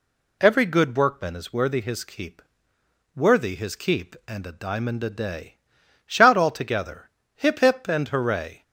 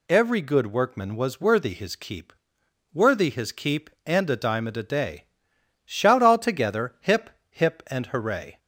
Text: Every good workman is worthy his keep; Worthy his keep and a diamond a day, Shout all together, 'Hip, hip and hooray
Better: first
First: none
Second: says "was" for "is"; at 1.1 s

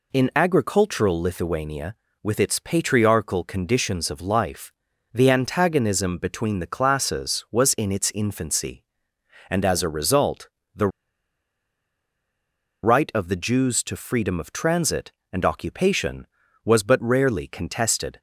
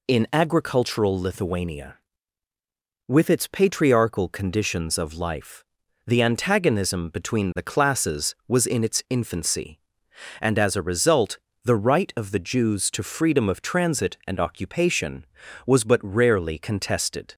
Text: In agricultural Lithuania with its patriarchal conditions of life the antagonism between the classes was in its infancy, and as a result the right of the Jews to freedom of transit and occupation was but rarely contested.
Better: second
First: pauses between "life" and "the"; at 4.7 s; 0.42 s long // pauses between "result" and "the"; slight; at 10.4 s; 0.26 s long // pauses between "the" and "right"; strong; at 10.8 s; 1.9 s long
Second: pauses between "life" and "the"; at 5.6 s; 0.44 s long // pauses between "result" and "the"; slight; at 11.3 s; 0.24 s long

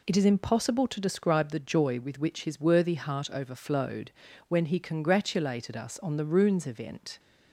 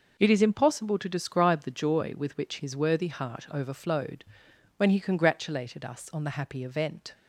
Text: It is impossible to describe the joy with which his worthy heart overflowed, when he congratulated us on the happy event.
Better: second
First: says "runes" for "happy"; at 6.2 s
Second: none

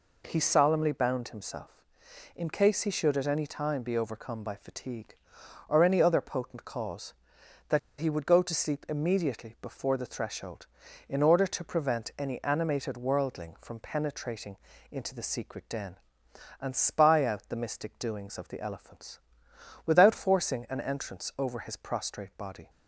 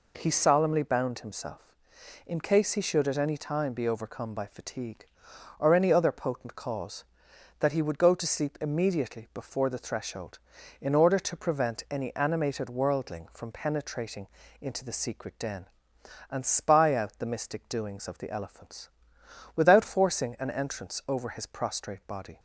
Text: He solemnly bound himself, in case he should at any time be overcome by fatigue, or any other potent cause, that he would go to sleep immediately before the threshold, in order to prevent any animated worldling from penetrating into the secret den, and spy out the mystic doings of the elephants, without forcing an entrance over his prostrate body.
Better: second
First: pauses between "that" and "he"; slight; at 7.7 s; 0.19 s long // pauses between "penetrating" and "into"; slight; at 14.5 s; 0.34 s long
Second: pauses between "penetrating" and "into"; slight; at 14.2 s; 0.33 s long

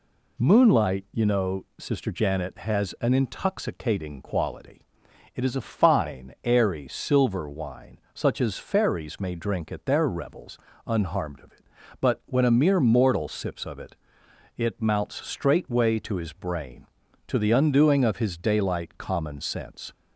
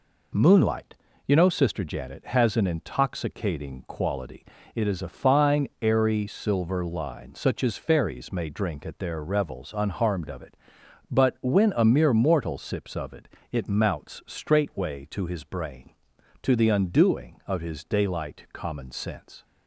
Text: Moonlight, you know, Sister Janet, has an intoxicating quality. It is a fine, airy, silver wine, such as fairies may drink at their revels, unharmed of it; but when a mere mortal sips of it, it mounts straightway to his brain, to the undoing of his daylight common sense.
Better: first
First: none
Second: says "line" for "wine"; at 6.8 s

